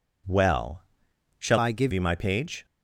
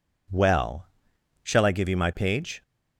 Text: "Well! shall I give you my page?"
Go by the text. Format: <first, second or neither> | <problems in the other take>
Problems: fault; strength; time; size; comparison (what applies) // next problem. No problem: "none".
second | changes voice from "I" to "give"; from 1.5 to 1.9 s; 0.4 s long